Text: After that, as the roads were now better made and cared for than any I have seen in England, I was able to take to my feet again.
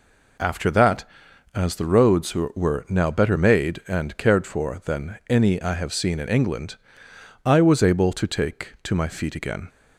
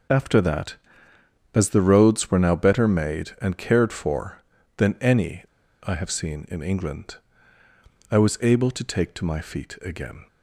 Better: first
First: none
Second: pauses between "any" and "I"; at 5.4 s; 0.38 s long

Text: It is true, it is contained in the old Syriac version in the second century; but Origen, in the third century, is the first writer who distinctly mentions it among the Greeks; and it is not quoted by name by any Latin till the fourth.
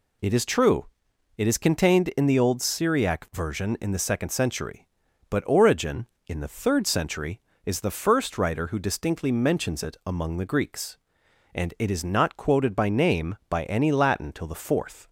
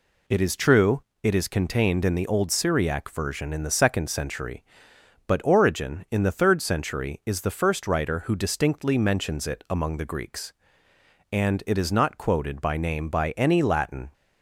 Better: first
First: none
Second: stops before "till the fourth"; at 14.1 s

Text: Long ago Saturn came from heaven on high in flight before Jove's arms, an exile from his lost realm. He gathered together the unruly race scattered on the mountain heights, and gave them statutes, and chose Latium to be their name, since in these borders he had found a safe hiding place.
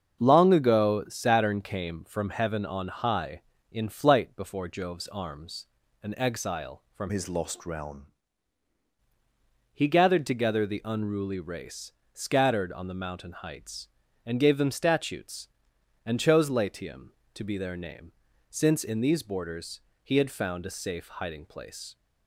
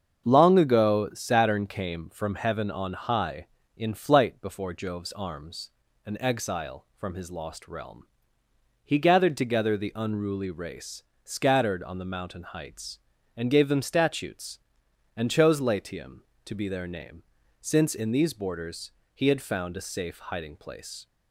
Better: second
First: starts louder than the rest; until 1.2 s; 7 dB // changes voice from "his" to "realm"; from 7.0 to 8.1 s; 1.1 s long // pauses between "race" and "scattered"; slight; at 11.9 s; 0.22 s long // pauses between "borders" and "he"; slight; at 19.8 s; 0.24 s long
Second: starts louder than the rest; until 1.3 s; 7 dB // pauses between "race" and "scattered"; slight; at 11.0 s; 0.22 s long // pauses between "borders" and "he"; slight; at 18.9 s; 0.24 s long

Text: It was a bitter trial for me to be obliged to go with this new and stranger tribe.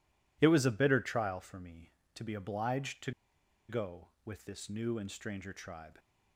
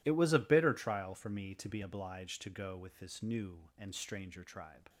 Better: second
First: pauses between "to" and "go"; noticeable; at 3.1 s; 0.58 s long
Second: none

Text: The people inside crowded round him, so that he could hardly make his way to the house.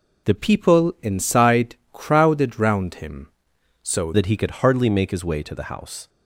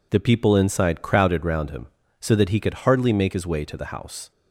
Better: second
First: changes voice from "people" to "so"; from 0.3 to 4.1 s; 3.8 s long // pauses between "inside" and "crowded"; slight; at 1.7 s; 0.16 s long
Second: none

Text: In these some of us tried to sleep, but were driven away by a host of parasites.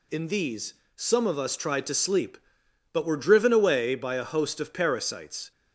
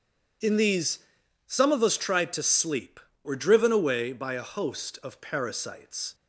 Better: first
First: pauses between "these" and "some"; slight; at 0.7 s; 0.22 s long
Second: pauses between "these" and "some"; noticeable; at 0.9 s; 0.48 s long // skips "but"; at 3.1 s

